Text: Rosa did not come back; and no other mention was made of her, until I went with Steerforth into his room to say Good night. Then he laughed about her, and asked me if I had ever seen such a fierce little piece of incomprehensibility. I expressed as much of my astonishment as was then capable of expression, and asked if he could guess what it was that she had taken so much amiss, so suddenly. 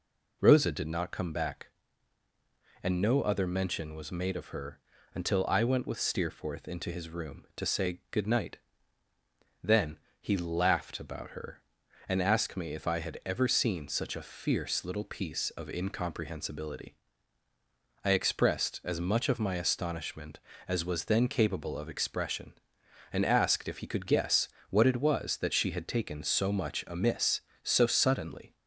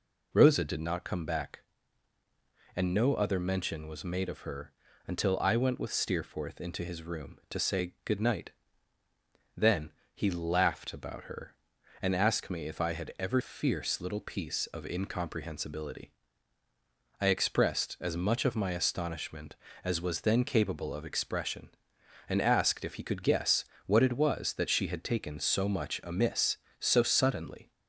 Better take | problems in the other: first | pauses between "Then" and "he"; slight; at 9.9 s; 0.22 s long; slight in the first // skips "seen such a"; at 13.4 s // pauses between "guess" and "what"; slight; at 23.6 s; 0.20 s long; slight in the first

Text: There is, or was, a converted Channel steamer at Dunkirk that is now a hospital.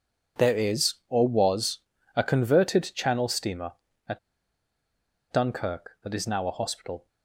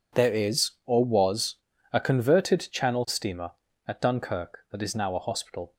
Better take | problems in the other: second | pauses between "at" and "Dunkirk"; at 4.1 s; 1.1 s long

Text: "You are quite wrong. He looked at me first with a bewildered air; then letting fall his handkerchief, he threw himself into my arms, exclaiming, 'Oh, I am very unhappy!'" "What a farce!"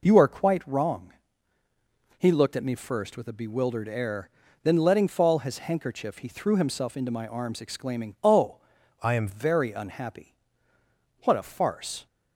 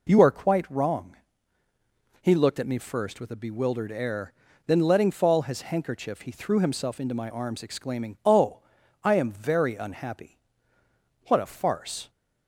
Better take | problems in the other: second | changes voice from "I" to "am"; from 9.0 to 9.2 s; 0.2 s long

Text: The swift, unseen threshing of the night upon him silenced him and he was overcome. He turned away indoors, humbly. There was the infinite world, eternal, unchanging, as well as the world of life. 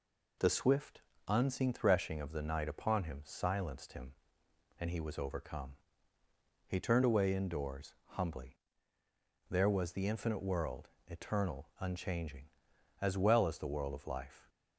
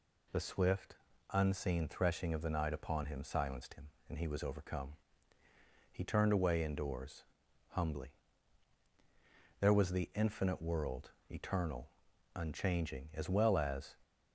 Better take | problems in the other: first | stops before "the world of life"; at 14.0 s

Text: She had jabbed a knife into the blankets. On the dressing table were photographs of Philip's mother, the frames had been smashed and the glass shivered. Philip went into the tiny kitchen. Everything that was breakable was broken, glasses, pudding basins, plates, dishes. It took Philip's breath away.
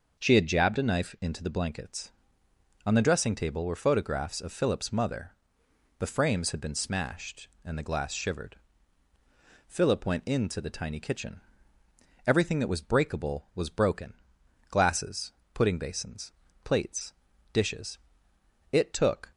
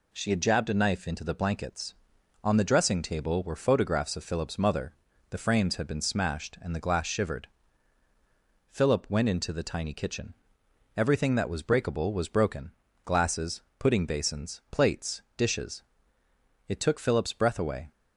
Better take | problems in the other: second | starts louder than the rest; noticeable; until 1.2 s; 6 dB // stops before "Philip's breath away"; at 19.3 s

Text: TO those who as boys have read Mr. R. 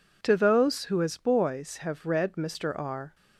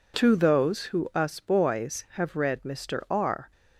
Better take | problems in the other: first | says "us" for "as"; at 1.1 s

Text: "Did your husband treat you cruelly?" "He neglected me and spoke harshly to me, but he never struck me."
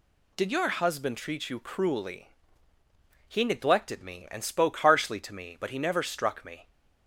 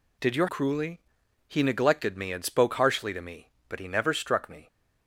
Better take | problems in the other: first | skips "husband treat you"; at 0.4 s

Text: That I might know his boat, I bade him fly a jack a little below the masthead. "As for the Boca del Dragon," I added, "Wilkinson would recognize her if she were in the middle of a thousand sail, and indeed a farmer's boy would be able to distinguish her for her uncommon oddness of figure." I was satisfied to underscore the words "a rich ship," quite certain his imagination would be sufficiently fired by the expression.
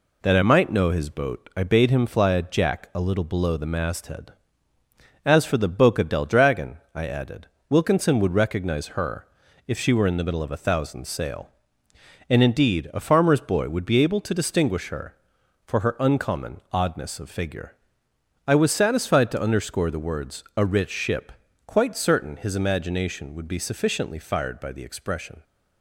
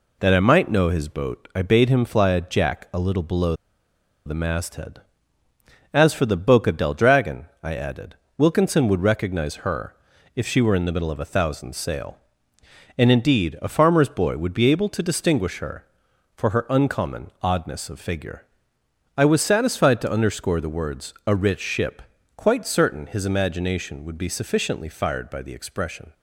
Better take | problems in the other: first | pauses between "below" and "the"; noticeable; at 3.5 s; 0.72 s long // pauses between "her" and "if"; at 9.9 s; 0.40 s long; also in the first

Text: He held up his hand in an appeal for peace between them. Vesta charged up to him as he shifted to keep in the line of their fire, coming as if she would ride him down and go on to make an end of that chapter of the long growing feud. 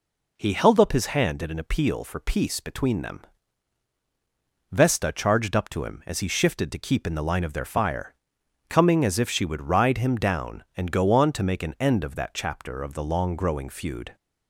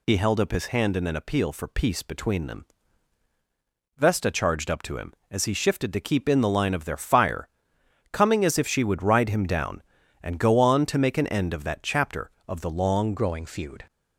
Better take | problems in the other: first | changes voice at "growing"; from 13.1 s on; 0.7 s long

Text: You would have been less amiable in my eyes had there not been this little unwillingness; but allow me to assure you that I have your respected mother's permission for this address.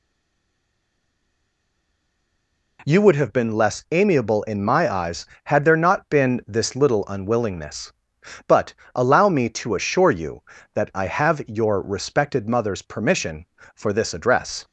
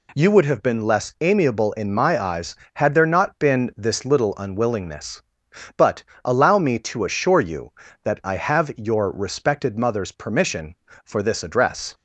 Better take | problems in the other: second | stays silent before the first word; strong; until 2.7 s; 2.7 s long // pauses between "but" and "allow"; slight; at 8.7 s; 0.22 s long; slight in the second

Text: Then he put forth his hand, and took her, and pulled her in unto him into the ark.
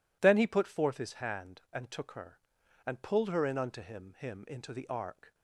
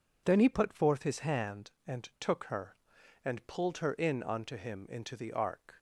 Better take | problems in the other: second | says "him" twice; at 4.1 s

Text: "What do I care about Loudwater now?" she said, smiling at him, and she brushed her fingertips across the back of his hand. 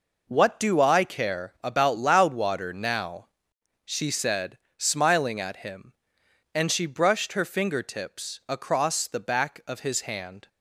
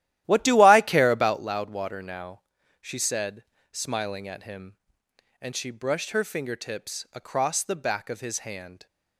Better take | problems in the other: first | starts louder than the rest; strong; until 1.4 s; 13.5 dB

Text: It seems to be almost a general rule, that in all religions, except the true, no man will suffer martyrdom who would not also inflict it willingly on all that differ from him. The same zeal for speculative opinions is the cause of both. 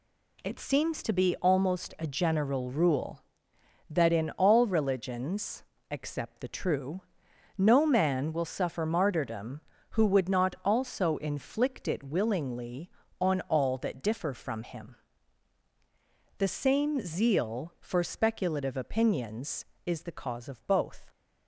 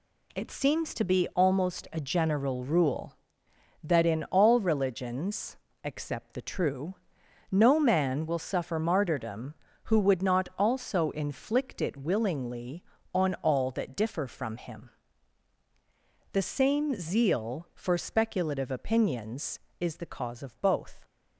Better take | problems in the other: neither | none

